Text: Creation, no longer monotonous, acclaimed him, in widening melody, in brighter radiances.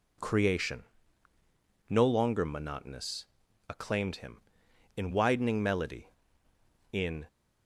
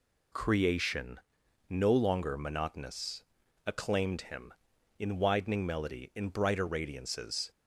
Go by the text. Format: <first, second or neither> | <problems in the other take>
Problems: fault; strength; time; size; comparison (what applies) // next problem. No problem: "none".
second | stops before "brighter radiances"; at 7.2 s